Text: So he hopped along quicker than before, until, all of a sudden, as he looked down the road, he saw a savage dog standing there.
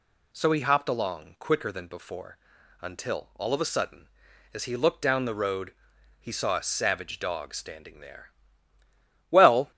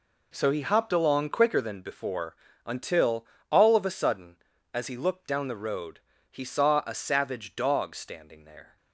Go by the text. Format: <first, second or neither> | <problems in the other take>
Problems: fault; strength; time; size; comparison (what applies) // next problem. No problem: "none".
second | goes on to say "Well"; slight; from 9.3 s on; 0.40 s long